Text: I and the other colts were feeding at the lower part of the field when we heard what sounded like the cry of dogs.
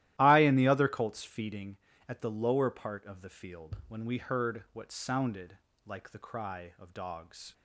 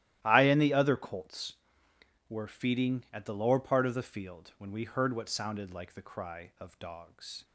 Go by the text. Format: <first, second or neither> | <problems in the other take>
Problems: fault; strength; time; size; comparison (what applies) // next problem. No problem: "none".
second | starts louder than the rest; strong; until 1.1 s; 14.5 dB; strong in the second // skips "were"; at 1.2 s // pauses between "sounded" and "like"; slight; at 5.5 s; 0.26 s long